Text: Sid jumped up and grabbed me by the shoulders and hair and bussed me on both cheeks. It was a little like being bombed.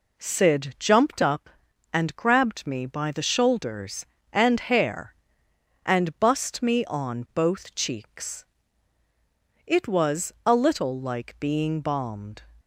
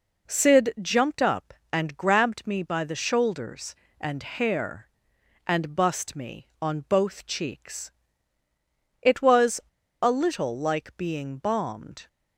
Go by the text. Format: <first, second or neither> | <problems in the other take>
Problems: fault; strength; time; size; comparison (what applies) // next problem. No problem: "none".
first | pauses between "was" and "a"; at 9.5 s; 0.42 s long